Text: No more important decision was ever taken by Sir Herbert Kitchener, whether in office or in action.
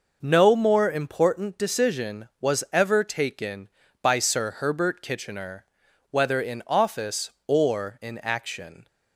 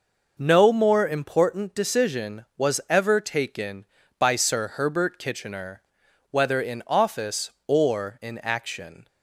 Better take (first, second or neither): neither